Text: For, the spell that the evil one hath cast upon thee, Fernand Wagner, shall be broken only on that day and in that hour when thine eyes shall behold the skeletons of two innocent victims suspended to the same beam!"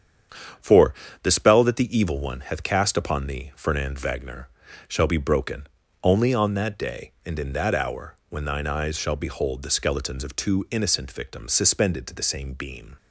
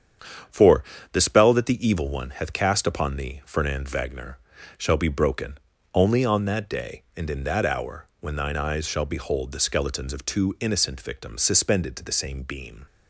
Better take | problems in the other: neither | starts louder than the rest; strong; the same in both // pauses between "broken" and "only"; slight; the same in both

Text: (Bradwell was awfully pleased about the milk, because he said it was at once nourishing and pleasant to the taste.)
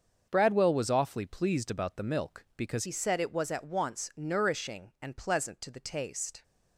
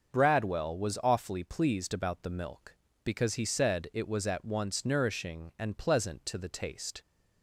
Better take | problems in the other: second | starts louder than the rest; until 1.3 s; 6.5 dB; also in the second // changes voice at "he"; from 2.8 s on; 3.6 s long

